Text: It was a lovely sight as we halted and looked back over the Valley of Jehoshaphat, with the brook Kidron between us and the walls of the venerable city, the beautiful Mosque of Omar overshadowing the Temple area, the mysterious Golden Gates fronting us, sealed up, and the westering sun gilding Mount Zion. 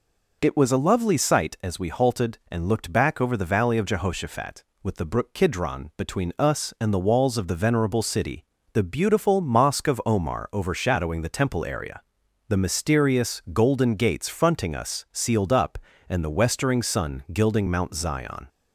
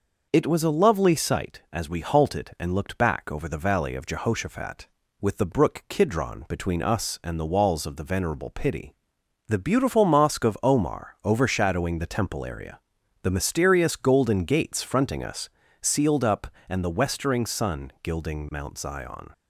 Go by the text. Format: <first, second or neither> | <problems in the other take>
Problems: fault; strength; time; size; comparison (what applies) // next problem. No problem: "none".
first | says "pity" for "city"; at 8.5 s